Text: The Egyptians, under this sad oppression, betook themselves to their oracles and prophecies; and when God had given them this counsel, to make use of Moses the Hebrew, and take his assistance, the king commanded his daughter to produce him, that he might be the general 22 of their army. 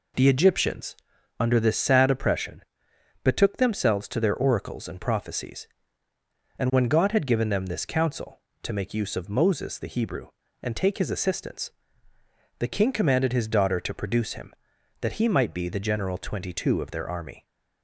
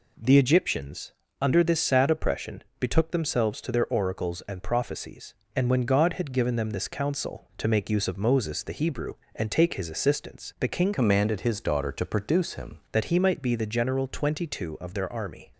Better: first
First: none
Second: changes voice from "commanded" to "him"; from 10.9 to 12.7 s; 1.8 s long

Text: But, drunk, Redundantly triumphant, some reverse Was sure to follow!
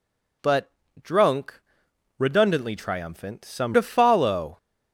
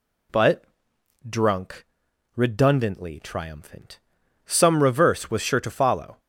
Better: second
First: skips "reverse Was sure"; at 3.7 s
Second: none

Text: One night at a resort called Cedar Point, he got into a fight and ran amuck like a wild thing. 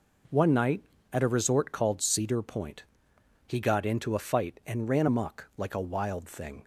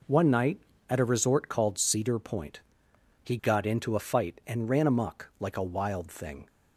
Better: neither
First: none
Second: none

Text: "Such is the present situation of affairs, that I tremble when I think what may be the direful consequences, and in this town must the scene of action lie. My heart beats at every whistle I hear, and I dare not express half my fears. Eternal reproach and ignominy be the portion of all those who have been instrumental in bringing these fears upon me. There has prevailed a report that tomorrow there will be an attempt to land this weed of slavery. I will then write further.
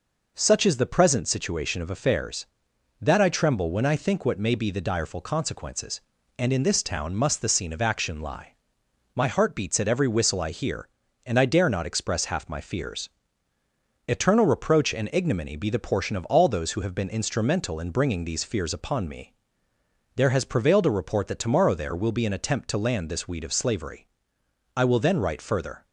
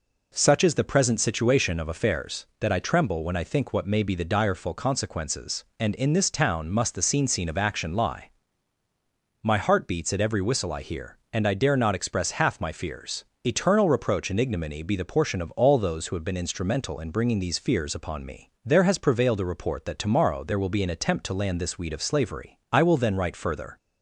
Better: first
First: none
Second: says "scene" twice; at 7.2 s

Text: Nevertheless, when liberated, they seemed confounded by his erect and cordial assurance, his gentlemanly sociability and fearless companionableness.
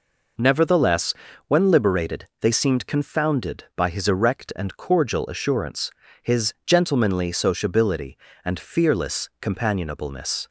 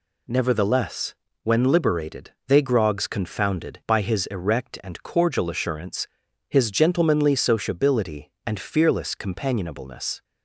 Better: first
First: none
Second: says "grogs" for "seemed"; at 2.6 s

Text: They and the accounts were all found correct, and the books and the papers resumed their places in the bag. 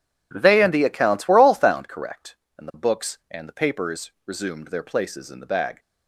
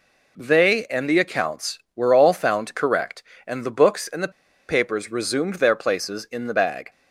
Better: first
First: none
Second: pauses between "the" and "papers"; at 4.3 s; 0.37 s long

